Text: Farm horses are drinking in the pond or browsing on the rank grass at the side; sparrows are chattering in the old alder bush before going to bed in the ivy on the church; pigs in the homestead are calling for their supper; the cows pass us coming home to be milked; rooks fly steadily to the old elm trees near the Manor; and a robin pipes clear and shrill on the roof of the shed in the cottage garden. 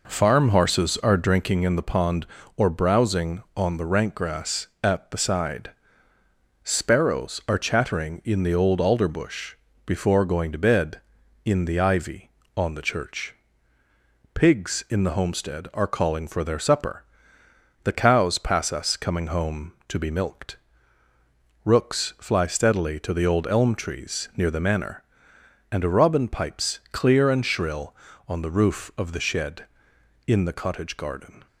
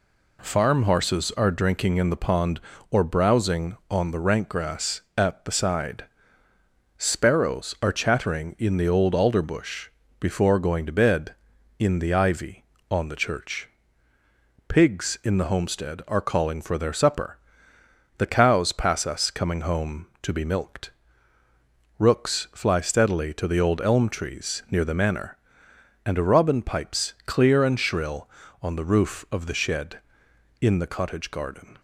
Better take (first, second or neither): second